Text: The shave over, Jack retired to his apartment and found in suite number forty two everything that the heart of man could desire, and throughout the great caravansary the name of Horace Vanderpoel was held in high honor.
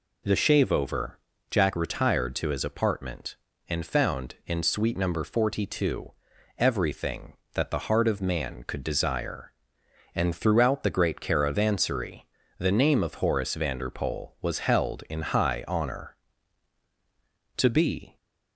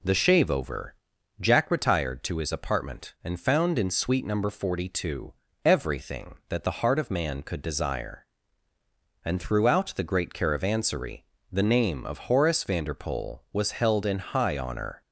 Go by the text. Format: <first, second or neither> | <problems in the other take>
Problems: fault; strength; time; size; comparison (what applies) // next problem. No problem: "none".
second | pauses between "two" and "everything"; noticeable; at 6.1 s; 0.46 s long; slight in the second // pauses between "caravansary" and "the"; slight; at 12.2 s; 0.36 s long; slight in the second // goes on to say "To be"; from 17.5 s on; 0.60 s long